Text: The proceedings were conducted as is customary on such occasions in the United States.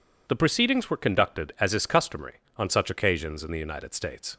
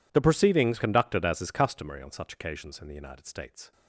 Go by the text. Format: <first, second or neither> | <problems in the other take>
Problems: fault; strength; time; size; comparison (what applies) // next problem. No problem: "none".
first | skips "were"; at 0.8 s